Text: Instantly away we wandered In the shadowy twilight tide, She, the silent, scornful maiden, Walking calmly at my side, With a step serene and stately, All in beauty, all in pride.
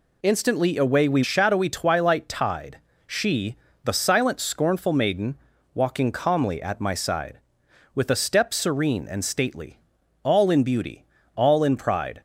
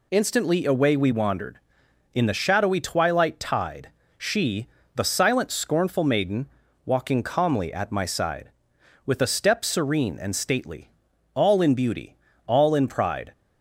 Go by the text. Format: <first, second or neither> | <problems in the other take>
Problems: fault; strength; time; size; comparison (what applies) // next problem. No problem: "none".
second | skips "wandered In the"; at 1.2 s